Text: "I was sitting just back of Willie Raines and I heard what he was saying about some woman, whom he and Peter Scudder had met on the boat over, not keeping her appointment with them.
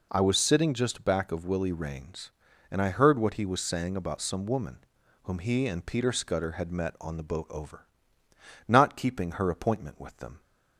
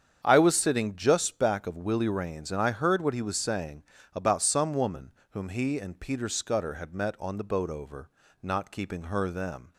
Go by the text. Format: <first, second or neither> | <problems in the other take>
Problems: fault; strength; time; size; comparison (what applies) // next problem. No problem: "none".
first | starts louder than the rest; strong; until 1.2 s; 8 dB // pauses between "saying" and "about"; slight; at 3.8 s; 0.32 s long // skips "appointment with"; at 9.2 s